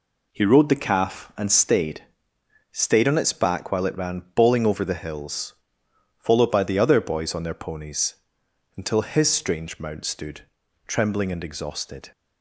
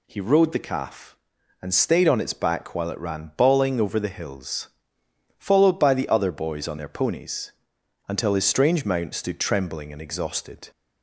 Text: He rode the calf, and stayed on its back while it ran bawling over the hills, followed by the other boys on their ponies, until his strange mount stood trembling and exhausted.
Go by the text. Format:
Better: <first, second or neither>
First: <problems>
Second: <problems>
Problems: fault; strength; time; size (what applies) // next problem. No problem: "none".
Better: second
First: says "stayed" twice; at 2.7 s // pauses between "stood" and "trembling"; noticeable; at 10.4 s; 0.46 s long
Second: none